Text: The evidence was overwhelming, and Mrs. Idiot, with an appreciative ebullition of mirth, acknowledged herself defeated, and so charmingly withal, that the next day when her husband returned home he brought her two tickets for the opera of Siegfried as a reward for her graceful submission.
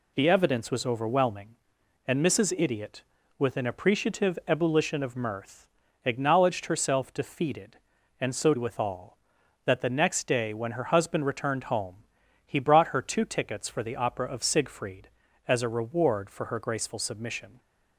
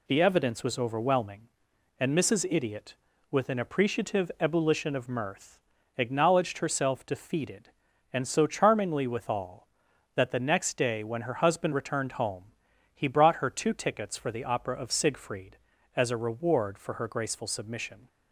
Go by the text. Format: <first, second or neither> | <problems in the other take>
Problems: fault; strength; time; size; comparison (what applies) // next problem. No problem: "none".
second | skips "charmingly"; at 8.5 s // pauses between "home" and "he"; noticeable; at 11.9 s; 0.52 s long; noticeable in the second